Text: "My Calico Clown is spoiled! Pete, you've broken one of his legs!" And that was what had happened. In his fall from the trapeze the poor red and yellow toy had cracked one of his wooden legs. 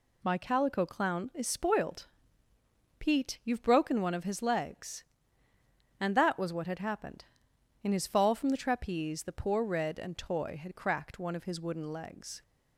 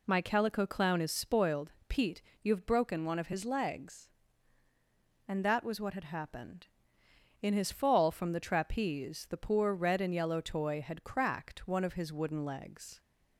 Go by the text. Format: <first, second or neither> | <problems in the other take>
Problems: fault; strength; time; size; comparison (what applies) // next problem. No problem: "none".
second | skips "yellow"; at 10.1 s